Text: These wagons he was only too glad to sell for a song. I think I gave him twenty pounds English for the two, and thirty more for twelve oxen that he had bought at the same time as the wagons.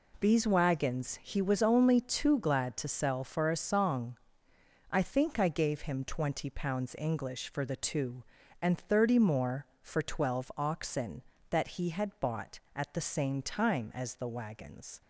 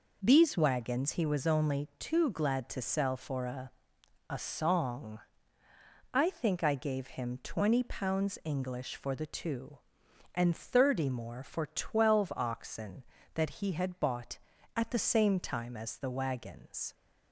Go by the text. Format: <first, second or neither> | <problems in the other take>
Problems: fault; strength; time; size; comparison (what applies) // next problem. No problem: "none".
first | says "a" twice; at 4.2 s